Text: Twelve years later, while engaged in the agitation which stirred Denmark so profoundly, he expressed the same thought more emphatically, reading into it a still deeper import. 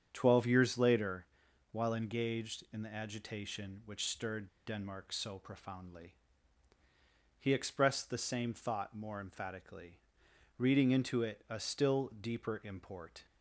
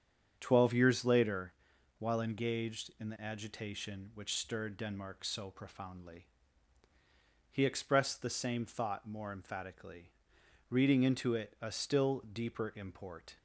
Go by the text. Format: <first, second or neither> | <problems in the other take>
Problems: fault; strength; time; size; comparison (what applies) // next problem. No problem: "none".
second | starts louder than the rest; strong; until 1.1 s; 8.5 dB; strong in the second // pauses between "stirred" and "Denmark"; slight; at 4.4 s; 0.18 s long